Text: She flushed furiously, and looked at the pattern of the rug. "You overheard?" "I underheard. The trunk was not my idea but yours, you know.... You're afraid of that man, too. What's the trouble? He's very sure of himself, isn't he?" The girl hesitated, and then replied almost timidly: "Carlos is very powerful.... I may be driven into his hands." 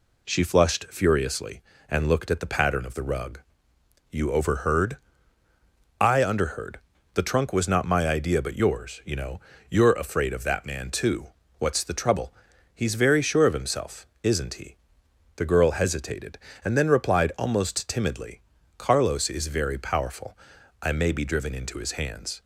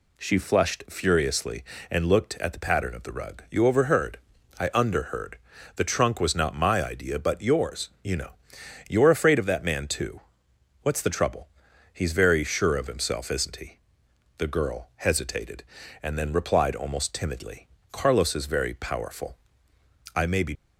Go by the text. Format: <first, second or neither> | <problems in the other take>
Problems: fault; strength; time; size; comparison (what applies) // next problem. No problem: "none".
first | stops before "driven into his hands"; at 20.5 s